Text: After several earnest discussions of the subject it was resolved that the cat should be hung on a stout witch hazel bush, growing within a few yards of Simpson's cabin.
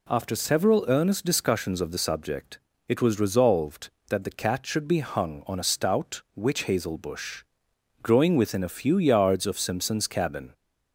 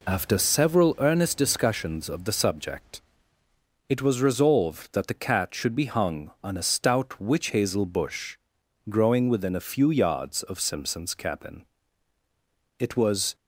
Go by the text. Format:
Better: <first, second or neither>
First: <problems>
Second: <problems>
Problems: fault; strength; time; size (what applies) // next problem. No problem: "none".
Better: first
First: pauses between "subject" and "it"; slight; at 2.5 s; 0.28 s long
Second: pauses between "subject" and "it"; noticeable; at 3.0 s; 0.86 s long // goes on to say "It was"; from 12.7 s on; 0.56 s long